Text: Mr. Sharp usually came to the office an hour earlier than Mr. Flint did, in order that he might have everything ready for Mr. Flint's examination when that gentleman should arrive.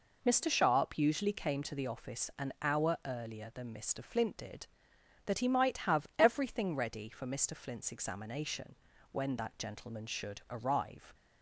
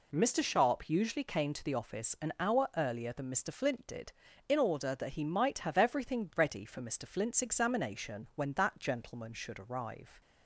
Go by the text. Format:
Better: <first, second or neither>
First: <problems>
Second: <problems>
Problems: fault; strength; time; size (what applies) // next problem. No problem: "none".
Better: second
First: skips "in order"; at 4.9 s // pauses between "examination" and "when"; slight; at 8.7 s; 0.36 s long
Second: none